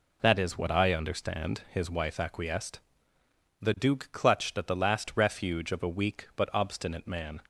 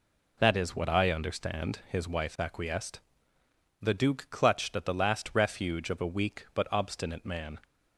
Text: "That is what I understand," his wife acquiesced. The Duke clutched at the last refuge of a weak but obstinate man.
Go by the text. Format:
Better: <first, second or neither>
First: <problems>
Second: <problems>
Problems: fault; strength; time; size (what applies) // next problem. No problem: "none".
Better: neither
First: none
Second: none